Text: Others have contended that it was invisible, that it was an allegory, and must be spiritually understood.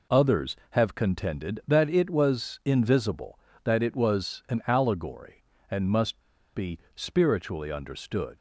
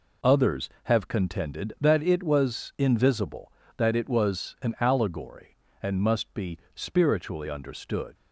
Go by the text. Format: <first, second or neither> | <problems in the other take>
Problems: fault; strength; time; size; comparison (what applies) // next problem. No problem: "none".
second | pauses between "must" and "be"; slight; at 6.2 s; 0.32 s long // pauses between "be" and "spiritually"; slight; at 6.7 s; 0.16 s long; slight in the second